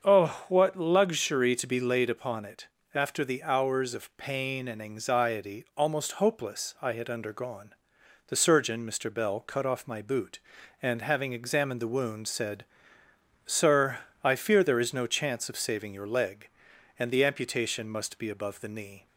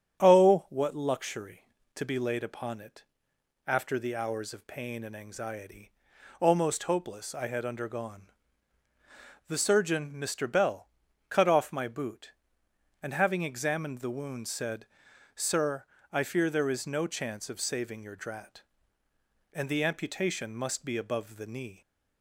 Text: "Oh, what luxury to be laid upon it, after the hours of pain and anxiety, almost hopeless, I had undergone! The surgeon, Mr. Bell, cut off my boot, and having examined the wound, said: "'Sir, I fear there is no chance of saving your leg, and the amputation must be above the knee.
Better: first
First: starts louder than the rest; until 1.0 s; 6.5 dB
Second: starts louder than the rest; strong; until 1.2 s; 8.5 dB // says "drat" for "leg"; at 18.1 s

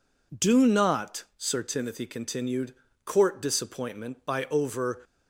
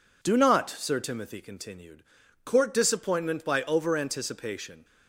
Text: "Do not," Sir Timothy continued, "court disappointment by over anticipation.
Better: second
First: stops before "anticipation"; at 5.0 s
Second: none

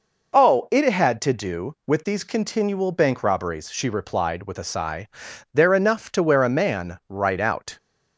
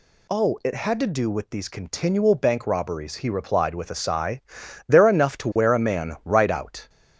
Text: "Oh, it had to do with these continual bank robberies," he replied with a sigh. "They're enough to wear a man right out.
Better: second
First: says "she" for "he"; at 3.7 s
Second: none

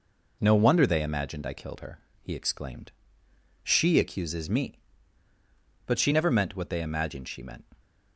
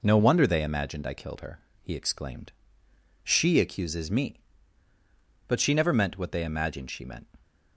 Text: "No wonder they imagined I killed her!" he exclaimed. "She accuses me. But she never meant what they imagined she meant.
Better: neither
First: none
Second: none

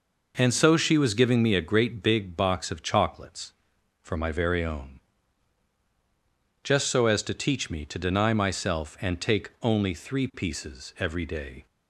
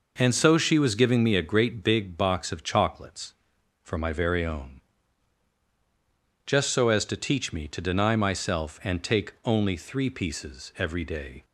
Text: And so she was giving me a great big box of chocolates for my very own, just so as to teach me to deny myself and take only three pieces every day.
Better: neither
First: none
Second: none

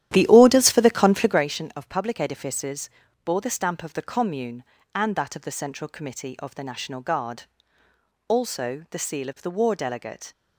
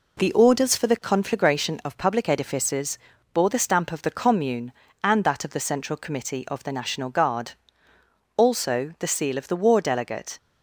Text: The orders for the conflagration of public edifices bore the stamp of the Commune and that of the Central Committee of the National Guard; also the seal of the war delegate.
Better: second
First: starts louder than the rest; strong; until 1.4 s; 12 dB // pauses between "edifices" and "bore"; slight; at 2.9 s; 0.34 s long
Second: pauses between "edifices" and "bore"; slight; at 2.9 s; 0.34 s long

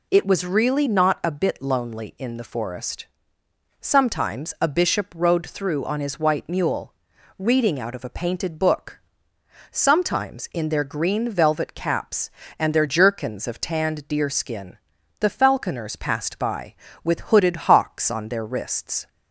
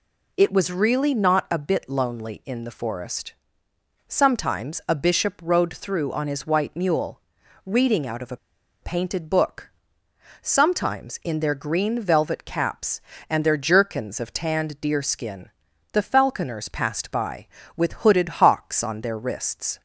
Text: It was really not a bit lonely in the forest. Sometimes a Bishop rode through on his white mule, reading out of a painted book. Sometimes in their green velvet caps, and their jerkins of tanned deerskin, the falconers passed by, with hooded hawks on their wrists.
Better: first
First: none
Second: pauses between "a" and "painted"; at 8.3 s; 0.44 s long

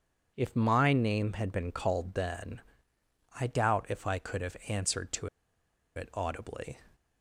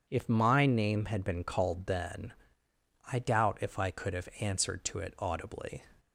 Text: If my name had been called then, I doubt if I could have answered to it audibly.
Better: second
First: pauses between "to" and "it"; noticeable; at 5.2 s; 0.68 s long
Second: none

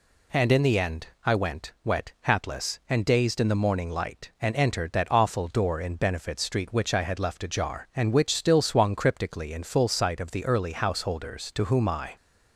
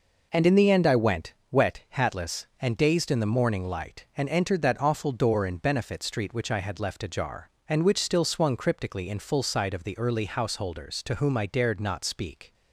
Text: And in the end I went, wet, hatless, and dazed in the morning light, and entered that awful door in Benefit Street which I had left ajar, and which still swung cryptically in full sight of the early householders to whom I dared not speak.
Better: second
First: pauses between "end" and "I"; slight; at 1.0 s; 0.18 s long // stops before "dared not speak"; at 12.1 s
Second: none

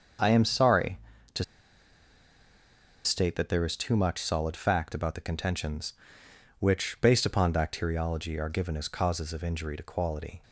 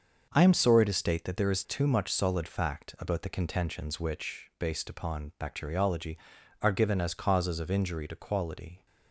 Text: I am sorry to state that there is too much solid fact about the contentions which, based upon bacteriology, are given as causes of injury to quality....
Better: second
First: starts louder than the rest; until 3.1 s; 6.5 dB // pauses between "to" and "state"; strong; at 1.4 s; 1.6 s long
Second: starts louder than the rest; until 1.3 s; 6.5 dB

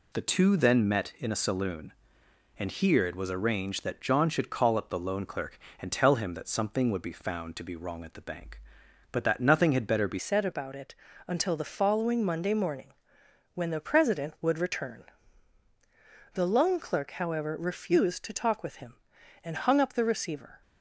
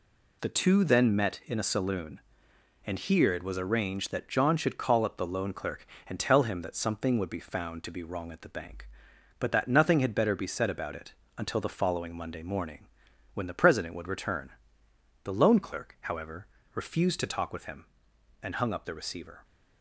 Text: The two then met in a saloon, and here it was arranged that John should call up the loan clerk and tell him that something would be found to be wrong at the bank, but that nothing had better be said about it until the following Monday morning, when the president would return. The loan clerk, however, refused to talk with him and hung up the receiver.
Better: second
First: changes voice at "said"; from 10.1 s on; 10.5 s long // pauses between "it" and "until"; slight; at 10.9 s; 0.32 s long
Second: pauses between "it" and "until"; slight; at 11.1 s; 0.24 s long

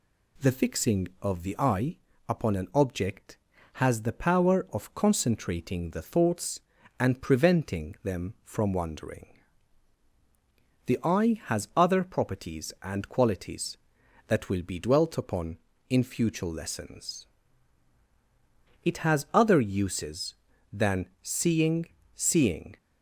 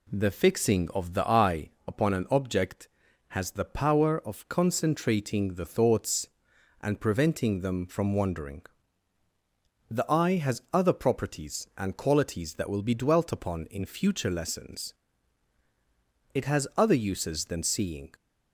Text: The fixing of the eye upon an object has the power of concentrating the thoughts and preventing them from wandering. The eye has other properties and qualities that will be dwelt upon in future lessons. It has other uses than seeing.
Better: second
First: pauses between "eye" and "upon"; slight; at 1.9 s; 0.32 s long // says "seeing" twice; at 22.1 s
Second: pauses between "eye" and "upon"; slight; at 1.6 s; 0.18 s long

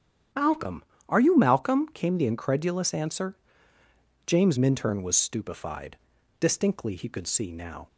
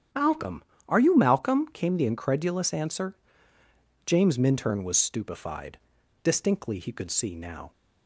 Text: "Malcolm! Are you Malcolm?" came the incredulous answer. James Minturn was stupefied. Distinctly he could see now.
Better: neither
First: starts louder than the rest; strong; until 1.6 s; 9 dB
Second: starts louder than the rest; strong; until 1.4 s; 9 dB

